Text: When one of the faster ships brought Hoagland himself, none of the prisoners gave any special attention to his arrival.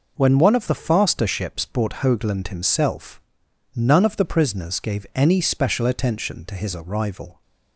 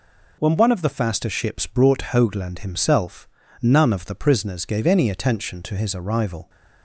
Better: first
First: none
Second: skips "special"; at 5.0 s

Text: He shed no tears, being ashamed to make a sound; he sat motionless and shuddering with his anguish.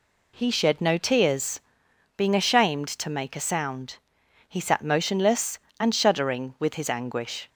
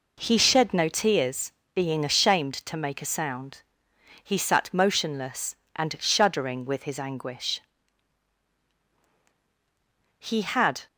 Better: first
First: none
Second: goes on to say "He had"; noticeable; from 10.1 s on; 0.68 s long

